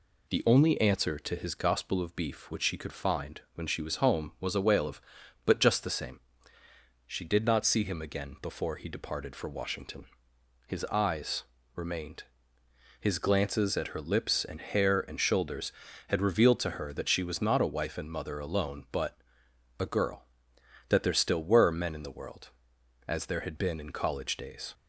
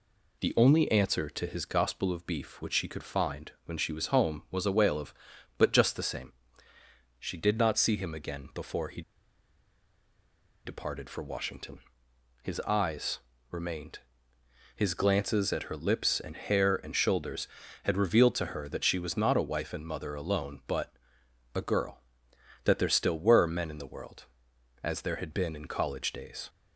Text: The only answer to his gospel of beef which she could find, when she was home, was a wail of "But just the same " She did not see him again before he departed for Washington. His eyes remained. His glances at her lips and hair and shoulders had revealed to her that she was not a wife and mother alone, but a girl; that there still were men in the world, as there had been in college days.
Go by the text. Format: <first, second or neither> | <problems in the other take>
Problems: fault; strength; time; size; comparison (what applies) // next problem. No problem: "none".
first | pauses between "he" and "departed"; strong; at 9.0 s; 1.6 s long // pauses between "eyes" and "remained"; slight; at 13.1 s; 0.32 s long; slight in the first // pauses between "but" and "a"; noticeable; at 20.9 s; 0.60 s long; noticeable in the first